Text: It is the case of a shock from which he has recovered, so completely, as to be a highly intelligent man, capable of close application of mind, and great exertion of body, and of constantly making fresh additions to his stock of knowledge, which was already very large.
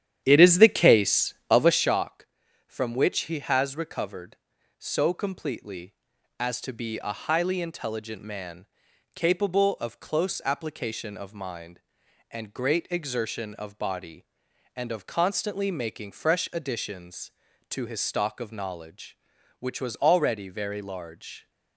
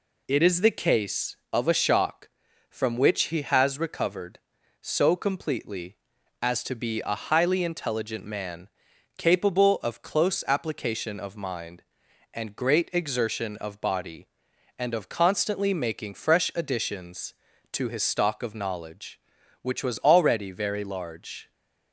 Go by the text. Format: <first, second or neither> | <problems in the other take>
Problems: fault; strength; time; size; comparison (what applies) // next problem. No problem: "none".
second | starts louder than the rest; strong; until 1.9 s; 10.5 dB